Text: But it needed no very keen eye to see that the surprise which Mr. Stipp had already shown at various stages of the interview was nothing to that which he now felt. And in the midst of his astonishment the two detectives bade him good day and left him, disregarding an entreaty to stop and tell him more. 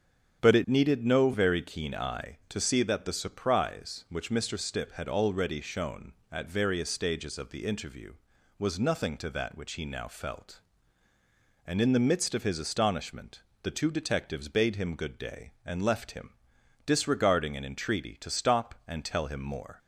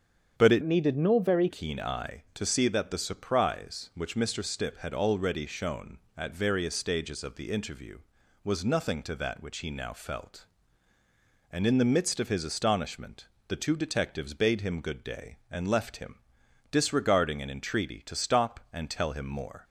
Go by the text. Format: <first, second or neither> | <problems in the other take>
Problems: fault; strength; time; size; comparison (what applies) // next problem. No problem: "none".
first | starts louder than the rest; strong; until 1.4 s; 8 dB; strong in the first // changes voice from "needed" to "very"; from 0.6 to 1.4 s; 0.8 s long // pauses between "astonishment" and "the"; slight; at 13.2 s; 0.20 s long; slight in the first